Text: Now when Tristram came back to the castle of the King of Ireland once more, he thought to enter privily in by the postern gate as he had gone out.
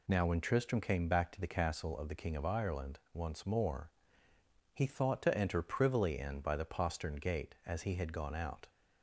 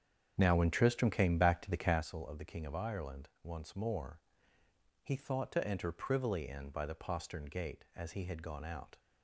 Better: first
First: none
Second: starts louder than the rest; strong; until 2.1 s; 8 dB

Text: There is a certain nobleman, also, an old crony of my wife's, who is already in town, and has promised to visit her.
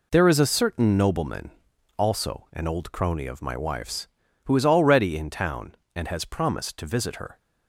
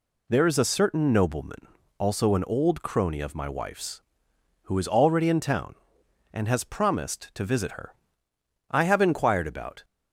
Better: first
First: none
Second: goes on to say "I have inquired about"; noticeable; from 8.6 s on; 1.1 s long

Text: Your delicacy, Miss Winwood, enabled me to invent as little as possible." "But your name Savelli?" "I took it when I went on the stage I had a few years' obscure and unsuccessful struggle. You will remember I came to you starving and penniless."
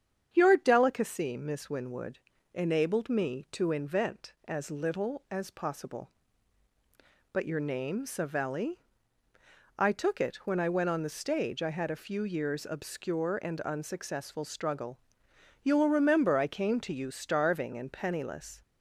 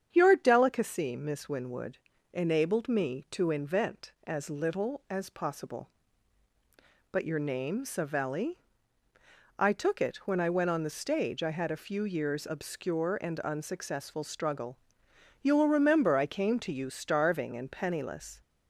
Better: neither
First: starts louder than the rest; strong; until 1.3 s; 8 dB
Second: starts louder than the rest; strong; until 1.1 s; 8 dB

